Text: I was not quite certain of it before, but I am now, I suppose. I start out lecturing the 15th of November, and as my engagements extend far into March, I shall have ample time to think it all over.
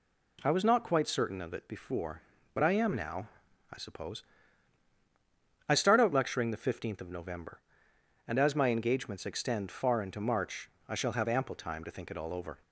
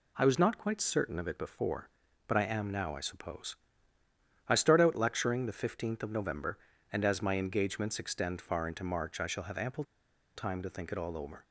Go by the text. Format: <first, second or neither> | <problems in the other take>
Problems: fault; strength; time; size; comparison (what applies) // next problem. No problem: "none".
first | pauses between "ample" and "time"; noticeable; at 9.8 s; 0.51 s long